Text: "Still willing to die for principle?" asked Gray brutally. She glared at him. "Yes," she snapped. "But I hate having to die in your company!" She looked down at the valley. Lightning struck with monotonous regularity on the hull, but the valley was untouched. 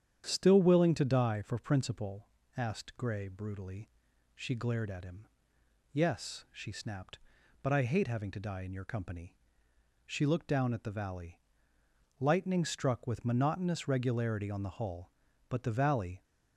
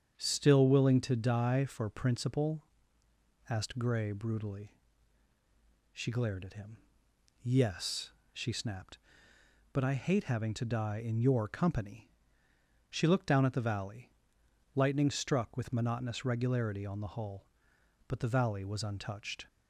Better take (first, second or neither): second